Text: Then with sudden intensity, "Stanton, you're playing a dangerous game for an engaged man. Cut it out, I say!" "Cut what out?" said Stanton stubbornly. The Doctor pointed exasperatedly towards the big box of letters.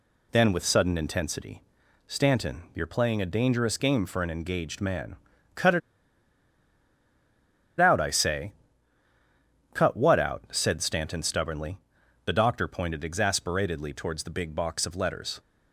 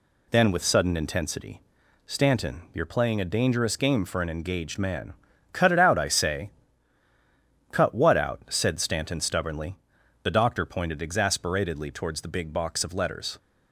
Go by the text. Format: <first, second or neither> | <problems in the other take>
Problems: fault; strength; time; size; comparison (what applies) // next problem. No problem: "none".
second | pauses between "it" and "out"; strong; at 5.8 s; 1.9 s long